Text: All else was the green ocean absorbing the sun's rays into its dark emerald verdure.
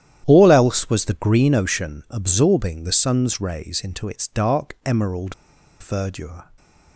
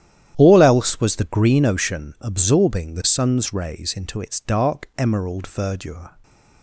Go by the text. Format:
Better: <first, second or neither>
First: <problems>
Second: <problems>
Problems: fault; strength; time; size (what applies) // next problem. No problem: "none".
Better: second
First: starts louder than the rest; strong; until 1.2 s; 11 dB // pauses between "emerald" and "verdure"; noticeable; at 5.3 s; 0.47 s long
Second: starts louder than the rest; strong; until 1.3 s; 11 dB